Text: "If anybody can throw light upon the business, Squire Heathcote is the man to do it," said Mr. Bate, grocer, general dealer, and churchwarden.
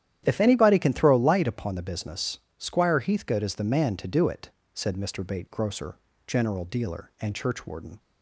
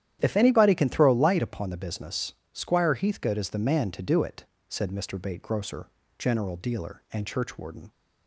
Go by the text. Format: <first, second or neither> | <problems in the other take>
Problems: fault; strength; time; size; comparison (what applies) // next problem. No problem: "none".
neither | starts louder than the rest; strong; the same in both